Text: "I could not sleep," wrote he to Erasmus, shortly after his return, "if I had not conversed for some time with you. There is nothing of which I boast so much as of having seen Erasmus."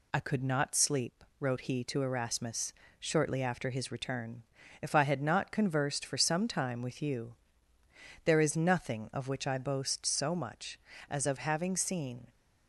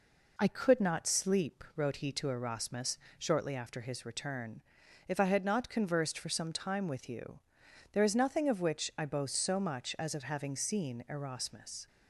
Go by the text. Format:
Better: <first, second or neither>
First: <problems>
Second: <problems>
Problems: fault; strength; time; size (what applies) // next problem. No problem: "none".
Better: second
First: stops before "Erasmus"; at 12.2 s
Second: none